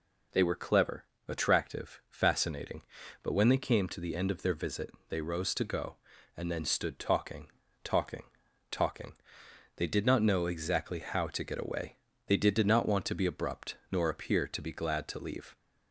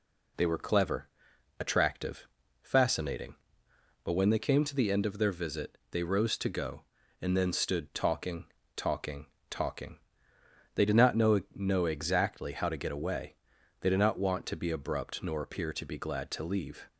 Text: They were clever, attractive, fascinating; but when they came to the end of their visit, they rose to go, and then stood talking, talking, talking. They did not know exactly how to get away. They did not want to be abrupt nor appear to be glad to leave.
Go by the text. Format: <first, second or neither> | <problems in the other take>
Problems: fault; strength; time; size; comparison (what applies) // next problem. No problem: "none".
first | says "know" twice; at 11.5 s